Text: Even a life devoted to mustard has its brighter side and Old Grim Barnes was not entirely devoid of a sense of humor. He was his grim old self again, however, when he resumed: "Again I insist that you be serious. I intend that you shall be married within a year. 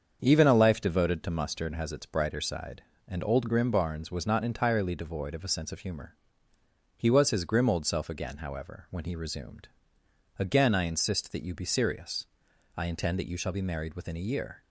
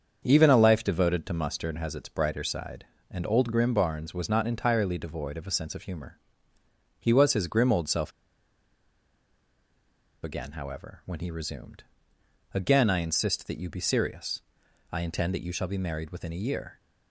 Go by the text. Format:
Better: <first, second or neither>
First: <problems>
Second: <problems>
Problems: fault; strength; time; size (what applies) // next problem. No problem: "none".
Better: first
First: starts louder than the rest; until 1.2 s; 7 dB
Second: starts louder than the rest; until 1.2 s; 7 dB // pauses between "self" and "again"; strong; at 8.1 s; 2.1 s long